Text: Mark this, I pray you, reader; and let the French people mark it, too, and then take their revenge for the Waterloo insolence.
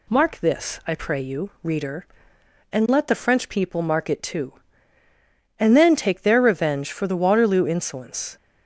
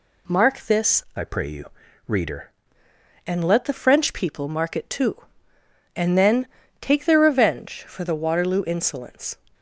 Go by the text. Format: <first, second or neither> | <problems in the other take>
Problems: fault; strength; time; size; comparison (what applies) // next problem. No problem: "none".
first | changes voice from "I" to "reader"; from 1.1 to 2.5 s; 1.4 s long // pauses between "then" and "take"; slight; at 6.4 s; 0.34 s long